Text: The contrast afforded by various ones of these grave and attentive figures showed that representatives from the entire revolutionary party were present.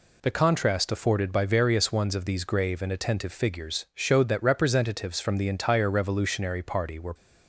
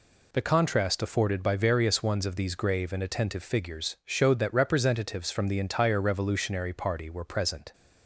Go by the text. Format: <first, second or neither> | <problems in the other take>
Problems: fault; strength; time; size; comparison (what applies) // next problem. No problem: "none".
second | stops before "present"; at 7.1 s